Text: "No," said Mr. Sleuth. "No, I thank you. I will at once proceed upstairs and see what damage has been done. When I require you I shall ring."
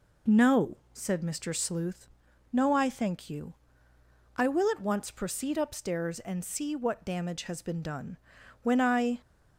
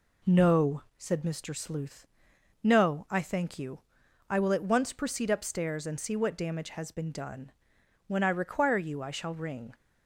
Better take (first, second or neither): second